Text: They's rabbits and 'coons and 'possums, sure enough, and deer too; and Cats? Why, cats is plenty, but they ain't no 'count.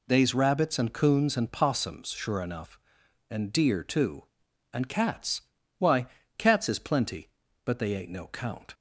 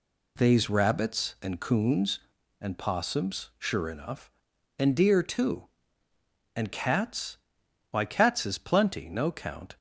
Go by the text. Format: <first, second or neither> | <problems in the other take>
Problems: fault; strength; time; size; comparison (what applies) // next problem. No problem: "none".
first | skips "but they ain't"; at 9.0 s